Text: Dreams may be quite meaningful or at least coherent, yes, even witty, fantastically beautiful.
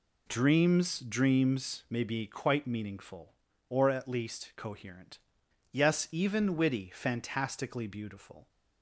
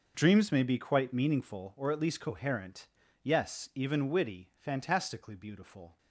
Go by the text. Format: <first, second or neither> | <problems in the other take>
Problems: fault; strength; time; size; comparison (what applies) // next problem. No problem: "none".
second | says "Dreams" twice; at 0.9 s